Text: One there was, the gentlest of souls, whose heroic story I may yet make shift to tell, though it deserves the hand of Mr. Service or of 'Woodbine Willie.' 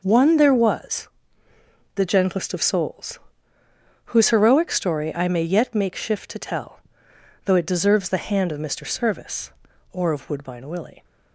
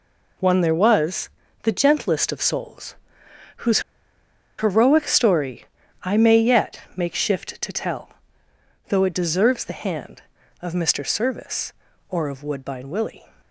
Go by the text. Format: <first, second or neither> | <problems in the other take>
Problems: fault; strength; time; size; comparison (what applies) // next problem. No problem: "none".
first | pauses between "whose" and "heroic"; noticeable; at 3.8 s; 0.77 s long // pauses between "story" and "I"; at 5.6 s; 0.38 s long // pauses between "yet" and "make"; slight; at 6.7 s; 0.16 s long